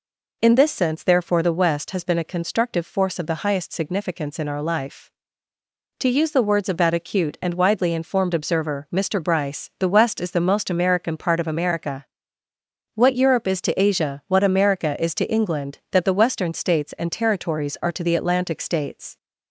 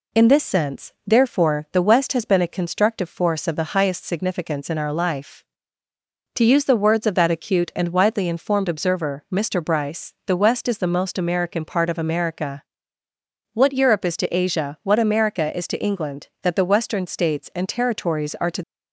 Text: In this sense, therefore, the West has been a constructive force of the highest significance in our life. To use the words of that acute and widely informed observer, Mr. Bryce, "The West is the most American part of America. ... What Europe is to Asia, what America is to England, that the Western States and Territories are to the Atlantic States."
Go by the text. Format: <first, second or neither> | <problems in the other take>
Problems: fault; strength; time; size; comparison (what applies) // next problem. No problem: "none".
first | stops before "the Atlantic States"; at 18.6 s